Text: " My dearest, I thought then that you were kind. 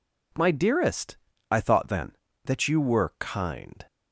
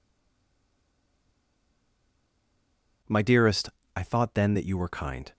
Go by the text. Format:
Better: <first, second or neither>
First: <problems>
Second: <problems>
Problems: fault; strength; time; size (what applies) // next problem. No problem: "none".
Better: first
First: none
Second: stays silent before the first word; strong; until 3.0 s; 3.0 s long